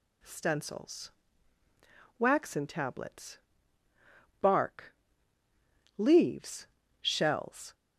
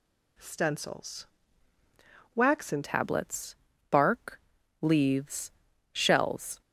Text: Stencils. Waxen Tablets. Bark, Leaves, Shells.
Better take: first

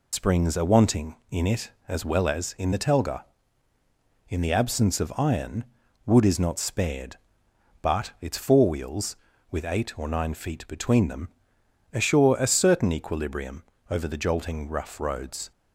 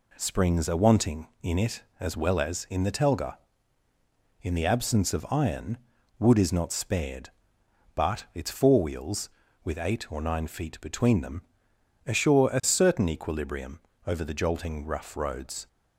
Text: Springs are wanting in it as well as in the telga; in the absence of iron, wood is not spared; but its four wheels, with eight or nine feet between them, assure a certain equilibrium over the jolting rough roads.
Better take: second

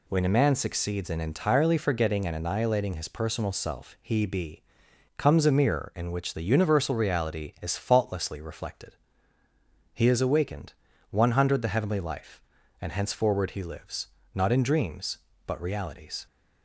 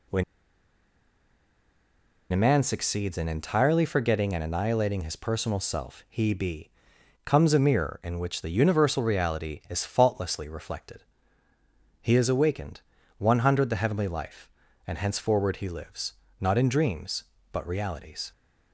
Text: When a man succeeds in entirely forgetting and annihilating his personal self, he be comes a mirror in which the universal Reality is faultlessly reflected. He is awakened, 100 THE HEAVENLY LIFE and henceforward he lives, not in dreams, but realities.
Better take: first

